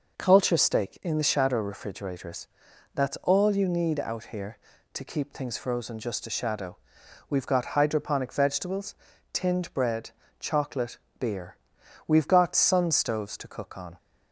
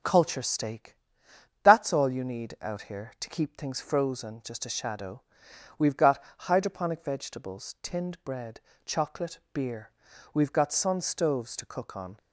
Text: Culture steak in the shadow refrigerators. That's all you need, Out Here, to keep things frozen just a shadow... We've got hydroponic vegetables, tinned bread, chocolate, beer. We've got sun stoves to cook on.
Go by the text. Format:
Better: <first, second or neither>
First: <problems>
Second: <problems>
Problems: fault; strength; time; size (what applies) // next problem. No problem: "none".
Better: first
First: none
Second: starts louder than the rest; until 1.7 s; 7 dB // skips "in the shadow refrigerators"; at 1.3 s // pauses between "got" and "hydroponic"; slight; at 6.2 s; 0.16 s long